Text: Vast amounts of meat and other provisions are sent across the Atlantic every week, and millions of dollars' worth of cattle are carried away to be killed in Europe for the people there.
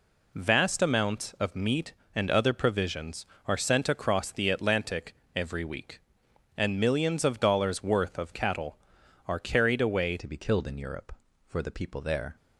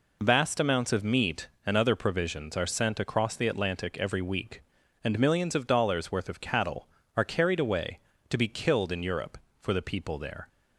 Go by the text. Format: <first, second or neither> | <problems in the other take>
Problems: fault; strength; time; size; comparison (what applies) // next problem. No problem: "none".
second | pauses between "Atlantic" and "every"; slight; at 5.1 s; 0.20 s long // changes voice at "to"; from 10.1 s on; 2.2 s long